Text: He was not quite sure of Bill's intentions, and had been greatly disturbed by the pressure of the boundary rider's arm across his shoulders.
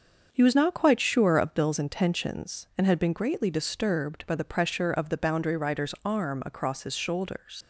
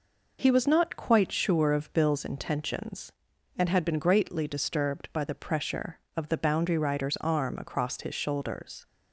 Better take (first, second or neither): second